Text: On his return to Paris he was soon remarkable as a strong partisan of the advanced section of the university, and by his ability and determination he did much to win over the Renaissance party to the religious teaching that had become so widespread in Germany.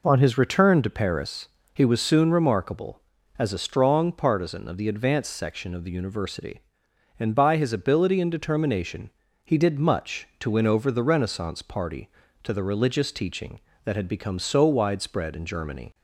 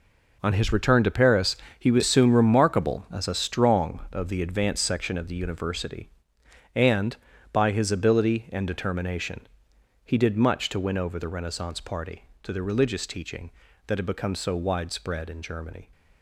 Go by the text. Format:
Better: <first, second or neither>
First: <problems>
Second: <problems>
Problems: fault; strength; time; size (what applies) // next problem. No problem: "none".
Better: first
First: pauses between "Paris" and "he"; slight; at 1.4 s; 0.24 s long // pauses between "determination" and "he"; slight; at 9.0 s; 0.36 s long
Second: pauses between "Paris" and "he"; slight; at 1.5 s; 0.22 s long // skips "partisan"; at 4.0 s // pauses between "determination" and "he"; noticeable; at 9.4 s; 0.64 s long